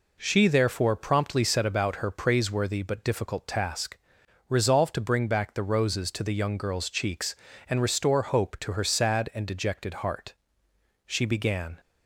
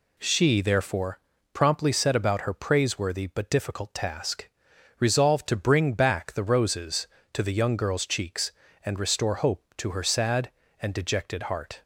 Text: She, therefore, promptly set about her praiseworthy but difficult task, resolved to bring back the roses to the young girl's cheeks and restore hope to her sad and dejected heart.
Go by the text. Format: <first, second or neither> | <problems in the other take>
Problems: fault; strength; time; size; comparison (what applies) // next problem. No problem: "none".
second | goes on to say "She began"; noticeable; from 11.0 s on; 0.72 s long